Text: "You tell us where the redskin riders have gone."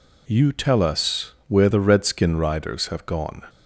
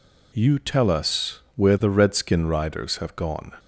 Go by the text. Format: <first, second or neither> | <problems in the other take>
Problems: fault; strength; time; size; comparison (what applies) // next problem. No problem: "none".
neither | pauses between "us" and "where"; slight; the same in both